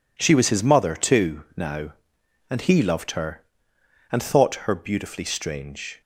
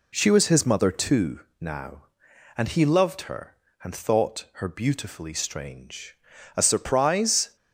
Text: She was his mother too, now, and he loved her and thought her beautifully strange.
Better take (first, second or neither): first